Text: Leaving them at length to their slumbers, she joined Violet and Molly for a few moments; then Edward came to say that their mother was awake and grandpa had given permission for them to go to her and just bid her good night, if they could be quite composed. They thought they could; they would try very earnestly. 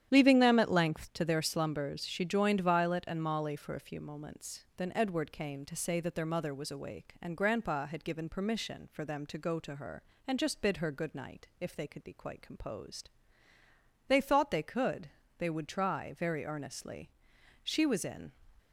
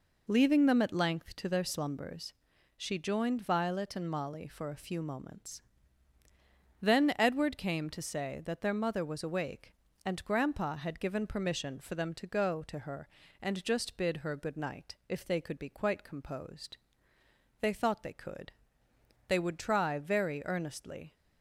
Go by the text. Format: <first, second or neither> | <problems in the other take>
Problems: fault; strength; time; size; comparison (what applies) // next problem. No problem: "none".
second | starts louder than the rest; strong; until 1.1 s; 10 dB // goes on to say "She was in"; noticeable; from 17.6 s on; 0.66 s long